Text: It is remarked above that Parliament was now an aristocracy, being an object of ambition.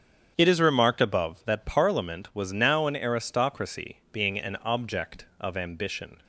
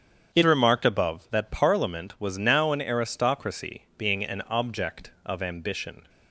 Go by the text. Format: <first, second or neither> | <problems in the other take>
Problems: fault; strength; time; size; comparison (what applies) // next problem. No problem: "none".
first | starts louder than the rest; strong; until 1.3 s; 8 dB; strong in the first // skips "is"; at 0.4 s